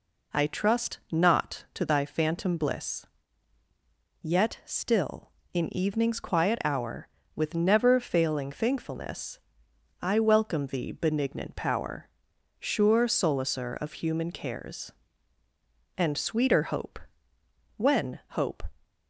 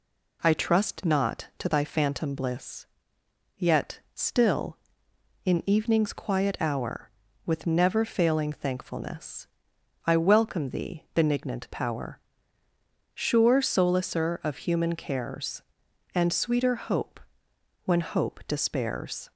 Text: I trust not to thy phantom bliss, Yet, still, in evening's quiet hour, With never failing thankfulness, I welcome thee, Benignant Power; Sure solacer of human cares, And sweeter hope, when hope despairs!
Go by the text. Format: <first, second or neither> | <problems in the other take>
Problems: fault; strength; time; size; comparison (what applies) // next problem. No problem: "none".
second | stops before "despairs"; at 18.8 s